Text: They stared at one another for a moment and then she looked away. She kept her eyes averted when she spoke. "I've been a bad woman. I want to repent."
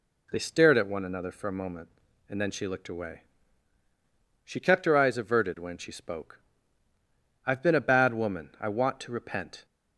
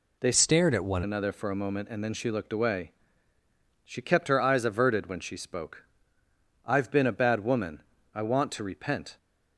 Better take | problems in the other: first | changes voice from "stared" to "one"; from 0.3 to 1.0 s; 0.7 s long

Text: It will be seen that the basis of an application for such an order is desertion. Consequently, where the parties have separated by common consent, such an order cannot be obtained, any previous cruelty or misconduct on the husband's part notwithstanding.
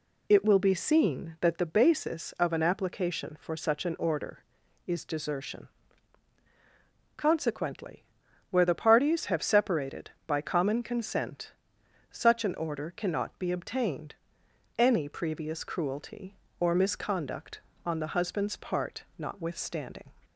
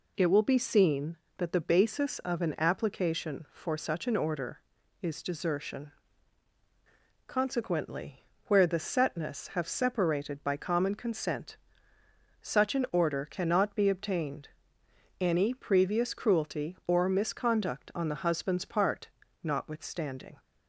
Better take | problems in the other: first | says "setness" for "parties"; at 8.7 s // pauses between "part" and "notwithstanding"; slight; at 19.0 s; 0.34 s long; slight in the first

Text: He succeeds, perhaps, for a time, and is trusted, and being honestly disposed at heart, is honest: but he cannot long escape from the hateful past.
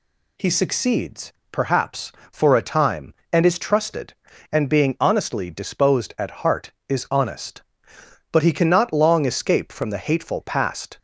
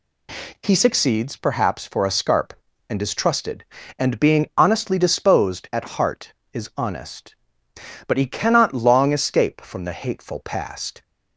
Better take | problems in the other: first | says "scarp" for "time"; at 2.1 s

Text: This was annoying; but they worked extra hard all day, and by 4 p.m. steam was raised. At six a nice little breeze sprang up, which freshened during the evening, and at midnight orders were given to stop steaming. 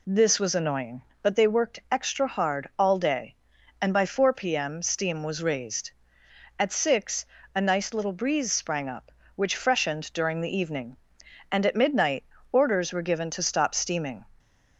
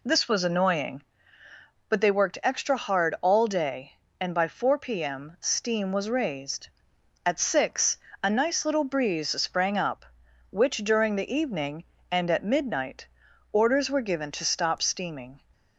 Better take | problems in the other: first | pauses between "six" and "a"; slight; at 7.9 s; 0.24 s long; slight in the first // skips "freshened"; at 10.7 s // pauses between "midnight" and "orders"; noticeable; at 13.0 s; 0.46 s long; slight in the first

